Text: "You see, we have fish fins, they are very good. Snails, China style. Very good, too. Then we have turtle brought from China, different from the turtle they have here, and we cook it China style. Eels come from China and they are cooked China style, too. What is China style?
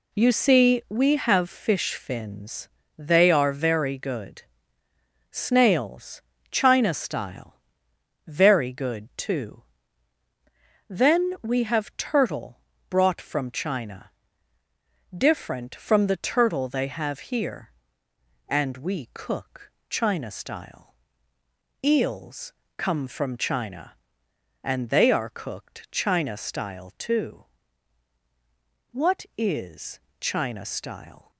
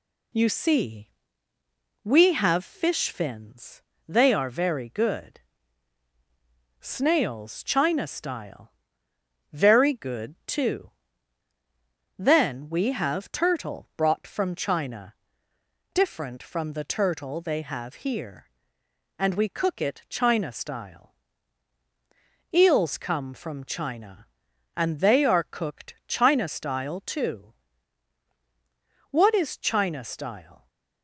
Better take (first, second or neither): second